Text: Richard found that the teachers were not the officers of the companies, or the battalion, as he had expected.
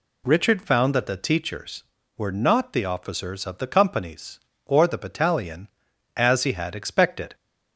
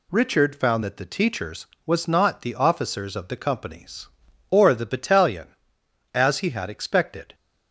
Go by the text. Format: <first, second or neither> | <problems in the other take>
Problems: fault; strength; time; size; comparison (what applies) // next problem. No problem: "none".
first | says "was" for "were"; at 1.8 s